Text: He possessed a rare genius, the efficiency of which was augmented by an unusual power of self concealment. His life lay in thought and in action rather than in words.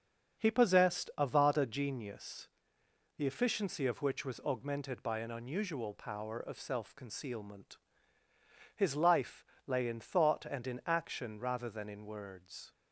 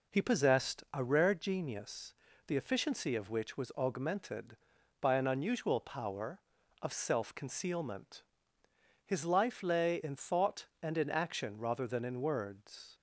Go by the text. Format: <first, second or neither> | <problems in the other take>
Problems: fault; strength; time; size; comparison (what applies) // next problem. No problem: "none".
second | starts louder than the rest; until 1.4 s; 6.5 dB // says "vada" for "rare"; at 1.2 s // pauses between "life" and "lay"; slight; at 9.4 s; 0.22 s long